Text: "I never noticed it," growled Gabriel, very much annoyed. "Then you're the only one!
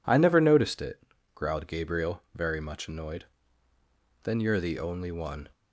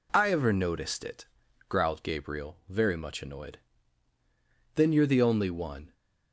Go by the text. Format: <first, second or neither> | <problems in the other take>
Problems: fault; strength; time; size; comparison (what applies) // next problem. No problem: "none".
first | says "ever" for "never"; at 0.3 s